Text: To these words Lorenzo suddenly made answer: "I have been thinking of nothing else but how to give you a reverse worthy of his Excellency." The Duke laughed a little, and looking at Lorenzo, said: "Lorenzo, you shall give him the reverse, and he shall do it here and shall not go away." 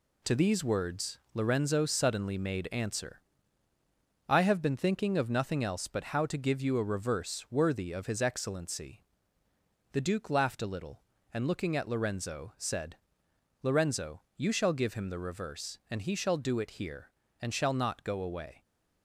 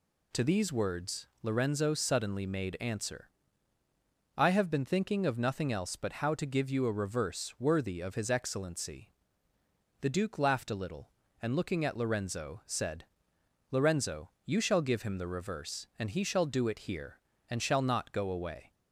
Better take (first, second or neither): second